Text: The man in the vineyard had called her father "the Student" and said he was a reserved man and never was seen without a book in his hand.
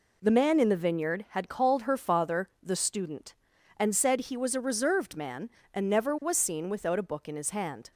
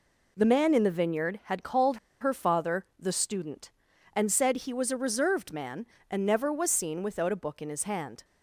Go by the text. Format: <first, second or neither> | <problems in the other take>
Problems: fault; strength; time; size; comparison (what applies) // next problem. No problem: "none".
first | pauses between "called" and "her"; slight; at 1.9 s; 0.24 s long